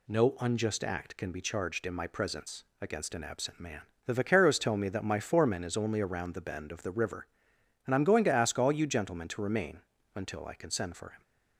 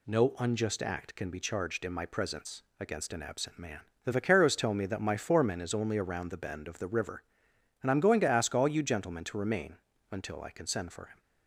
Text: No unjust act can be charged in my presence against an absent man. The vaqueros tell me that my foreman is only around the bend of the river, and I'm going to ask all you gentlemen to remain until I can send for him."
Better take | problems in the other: neither | pauses between "presence" and "against"; slight; the same in both // pauses between "remain" and "until"; slight; the same in both

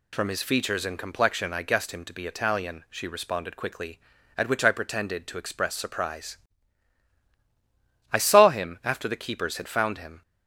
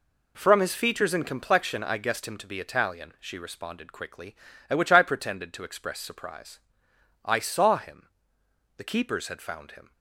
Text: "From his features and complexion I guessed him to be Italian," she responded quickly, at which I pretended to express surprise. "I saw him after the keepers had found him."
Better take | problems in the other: first | skips "after"; at 8.4 s

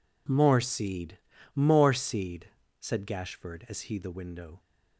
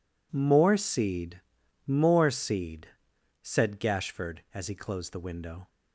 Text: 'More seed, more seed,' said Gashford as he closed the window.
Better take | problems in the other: second | skips "closed"; at 3.9 s

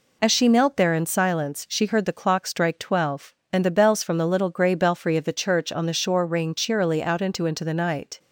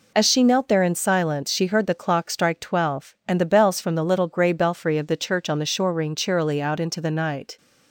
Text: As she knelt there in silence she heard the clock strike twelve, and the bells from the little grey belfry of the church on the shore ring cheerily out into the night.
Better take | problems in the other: second | says "into" twice; at 7.4 s

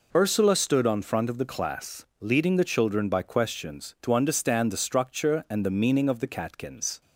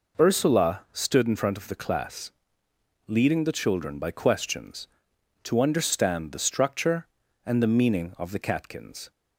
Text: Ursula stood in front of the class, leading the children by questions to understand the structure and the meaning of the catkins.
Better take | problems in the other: second | says "on" for "in"; at 0.8 s

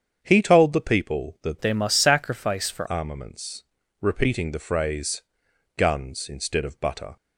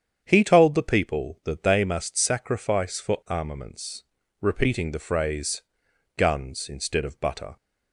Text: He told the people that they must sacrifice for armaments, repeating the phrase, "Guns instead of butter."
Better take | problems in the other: second | starts louder than the rest; strong; until 1.2 s; 8 dB; strong in the second // changes voice from "they" to "for"; from 1.6 to 2.8 s; 1.2 s long

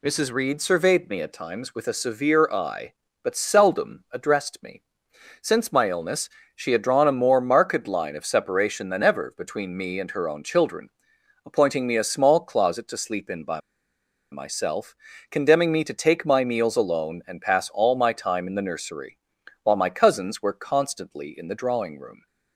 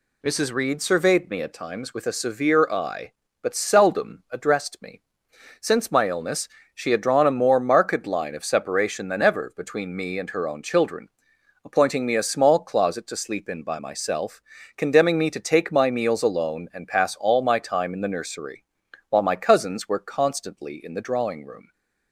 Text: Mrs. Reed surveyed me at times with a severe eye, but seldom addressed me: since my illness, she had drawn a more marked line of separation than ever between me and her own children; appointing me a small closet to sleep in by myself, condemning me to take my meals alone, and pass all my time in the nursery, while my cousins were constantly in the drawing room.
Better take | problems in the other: second | pauses between "by" and "myself"; noticeable; at 13.5 s; 0.73 s long

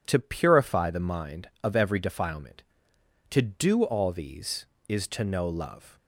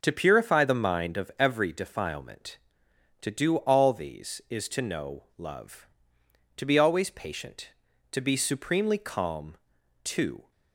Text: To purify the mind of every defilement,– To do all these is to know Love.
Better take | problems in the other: first | starts louder than the rest; until 1.0 s; 6 dB // goes on to say "To be always patient To be supremely calm To"; strong; from 6.5 s on; 3.9 s long

